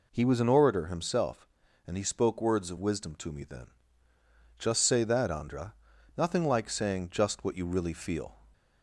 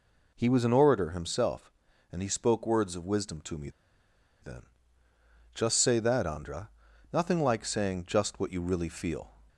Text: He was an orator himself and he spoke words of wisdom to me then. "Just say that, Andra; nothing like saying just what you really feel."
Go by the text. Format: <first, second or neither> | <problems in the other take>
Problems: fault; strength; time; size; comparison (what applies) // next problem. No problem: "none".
first | pauses between "me" and "then"; noticeable; at 3.6 s; 0.72 s long